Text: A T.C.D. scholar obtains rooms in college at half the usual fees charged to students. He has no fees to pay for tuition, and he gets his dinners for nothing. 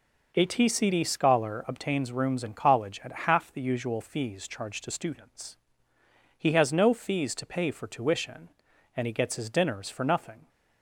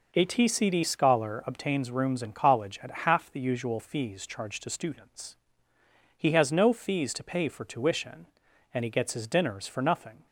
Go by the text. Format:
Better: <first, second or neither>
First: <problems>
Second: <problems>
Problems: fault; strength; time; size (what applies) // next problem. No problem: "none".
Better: neither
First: none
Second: none